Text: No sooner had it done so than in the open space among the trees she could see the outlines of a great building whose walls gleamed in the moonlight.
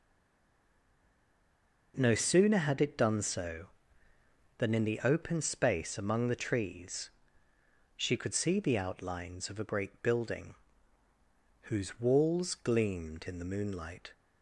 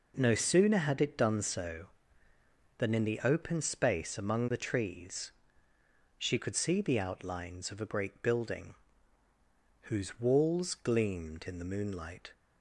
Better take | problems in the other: second | stays silent before the first word; noticeable; until 1.9 s; 1.9 s long // pauses between "trees" and "she"; noticeable; at 7.0 s; 0.86 s long; noticeable in the second // pauses between "building" and "whose"; at 10.5 s; 1.1 s long; also in the second

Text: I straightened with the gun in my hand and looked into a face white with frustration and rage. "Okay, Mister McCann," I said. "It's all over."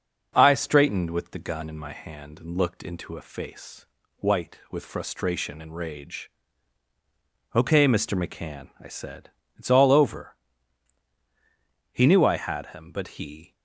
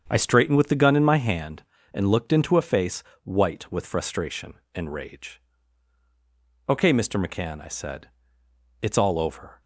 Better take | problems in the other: second | starts louder than the rest; noticeable; until 1.3 s; 6 dB; strong in the second // pauses between "face" and "white"; slight; at 3.8 s; 0.30 s long; slight in the second // goes on to say "He knew I had him but he"; from 11.9 s on; 1.6 s long

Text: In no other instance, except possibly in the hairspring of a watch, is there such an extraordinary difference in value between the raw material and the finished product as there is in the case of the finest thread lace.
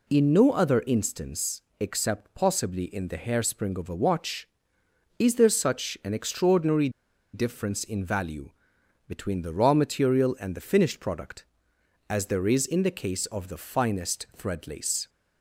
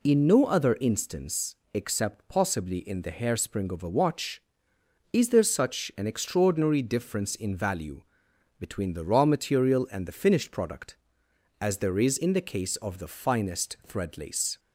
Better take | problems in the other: second | pauses between "extraordinary" and "difference"; at 6.8 s; 0.44 s long // pauses between "value" and "between"; noticeable; at 8.5 s; 0.58 s long; noticeable in the second

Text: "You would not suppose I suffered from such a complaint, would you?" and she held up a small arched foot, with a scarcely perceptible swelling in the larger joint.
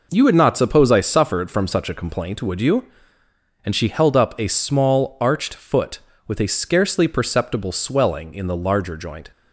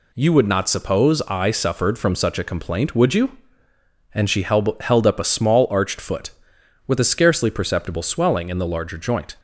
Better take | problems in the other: first | says "held" twice; at 4.8 s

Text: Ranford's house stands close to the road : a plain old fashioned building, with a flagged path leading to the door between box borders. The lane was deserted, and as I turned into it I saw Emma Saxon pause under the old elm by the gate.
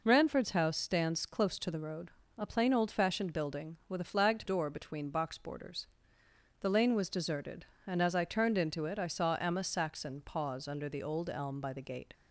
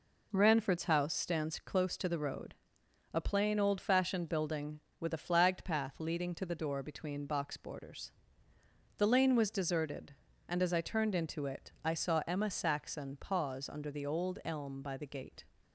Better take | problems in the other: second | skips "path leading to the"; at 4.4 s

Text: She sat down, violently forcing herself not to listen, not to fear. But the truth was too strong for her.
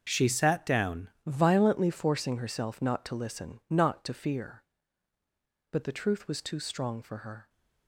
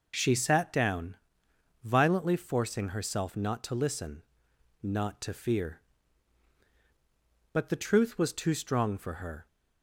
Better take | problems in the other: second | starts louder than the rest; until 1.1 s; 6.5 dB // changes voice at "violently"; from 1.2 s on; 6.2 s long

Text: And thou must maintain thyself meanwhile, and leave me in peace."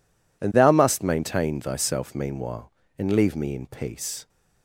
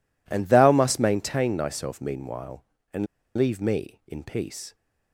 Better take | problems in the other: first | pauses between "and" and "leave"; slight; at 3.0 s; 0.30 s long

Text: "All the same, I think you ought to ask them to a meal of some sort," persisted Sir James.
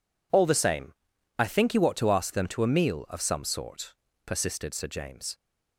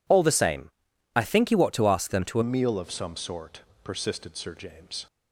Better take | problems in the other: first | changes voice at "meal"; from 2.4 s on; 2.6 s long

